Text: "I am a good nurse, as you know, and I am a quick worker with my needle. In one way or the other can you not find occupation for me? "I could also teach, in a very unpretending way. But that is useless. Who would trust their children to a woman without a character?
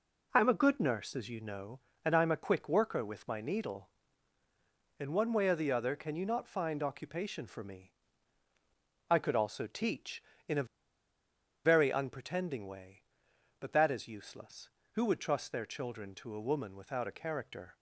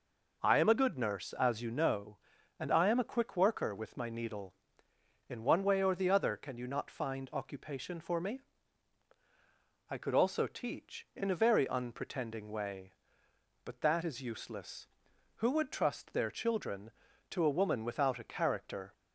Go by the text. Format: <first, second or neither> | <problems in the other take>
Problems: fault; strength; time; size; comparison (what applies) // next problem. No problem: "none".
second | pauses between "a" and "very"; at 10.6 s; 1.0 s long